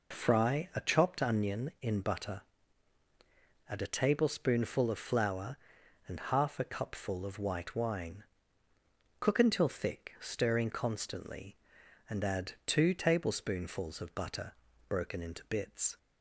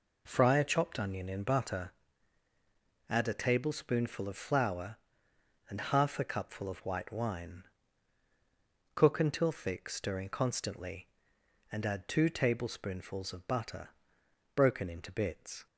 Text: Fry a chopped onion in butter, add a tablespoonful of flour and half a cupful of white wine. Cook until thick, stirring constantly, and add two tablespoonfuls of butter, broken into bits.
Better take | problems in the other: neither | none

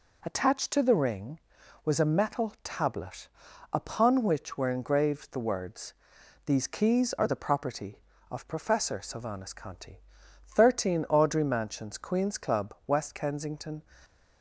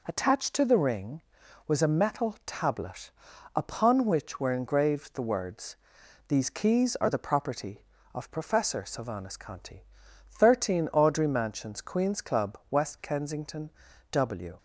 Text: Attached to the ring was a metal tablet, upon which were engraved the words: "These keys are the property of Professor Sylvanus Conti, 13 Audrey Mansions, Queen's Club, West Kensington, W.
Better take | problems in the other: second | stops before "W"; at 14.0 s

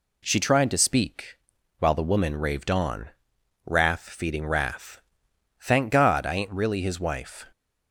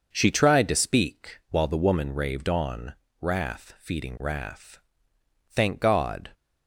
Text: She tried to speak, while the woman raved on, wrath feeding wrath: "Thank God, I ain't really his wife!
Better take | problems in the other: first | starts louder than the rest; noticeable; until 1.1 s; 6 dB // stops before "I ain't really his wife"; at 6.3 s

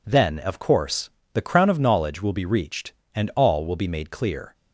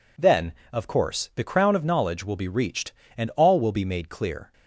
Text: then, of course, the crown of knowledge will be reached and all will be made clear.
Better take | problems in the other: neither | none

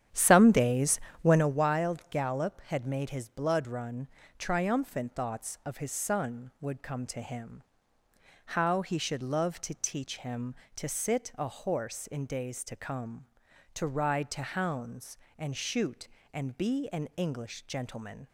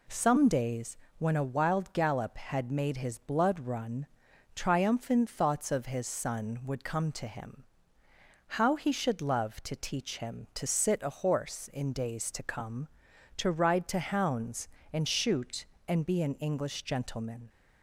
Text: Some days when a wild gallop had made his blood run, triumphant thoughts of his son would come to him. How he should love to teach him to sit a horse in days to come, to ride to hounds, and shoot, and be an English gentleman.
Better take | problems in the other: second | starts louder than the rest; strong; until 1.6 s; 9.5 dB // pauses between "days" and "when"; slight; at 0.9 s; 0.24 s long; slight in the second

